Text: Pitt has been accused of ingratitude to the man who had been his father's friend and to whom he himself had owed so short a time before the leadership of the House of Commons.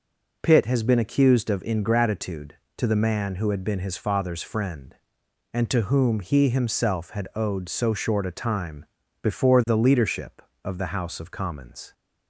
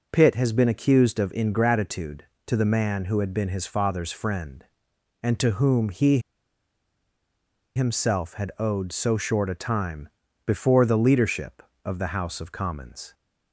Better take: first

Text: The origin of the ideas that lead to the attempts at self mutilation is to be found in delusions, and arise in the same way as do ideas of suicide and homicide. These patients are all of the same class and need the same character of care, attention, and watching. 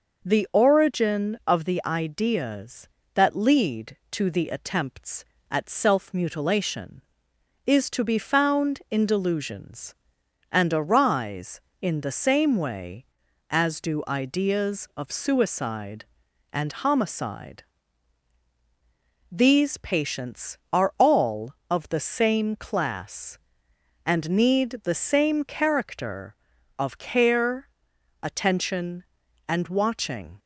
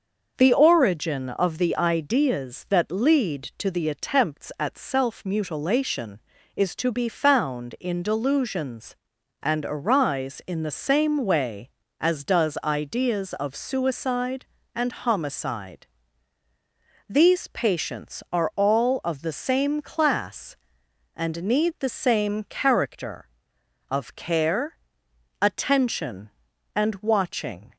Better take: first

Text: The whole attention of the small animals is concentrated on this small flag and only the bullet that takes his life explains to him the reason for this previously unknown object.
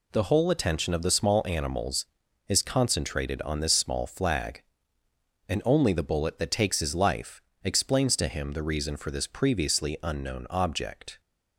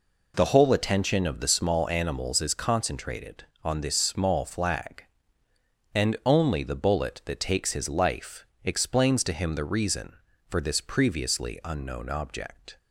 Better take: neither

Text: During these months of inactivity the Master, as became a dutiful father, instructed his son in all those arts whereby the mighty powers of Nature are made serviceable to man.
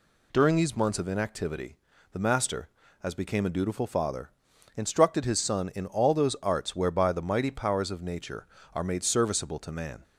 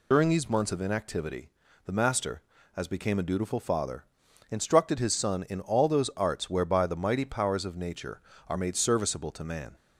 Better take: first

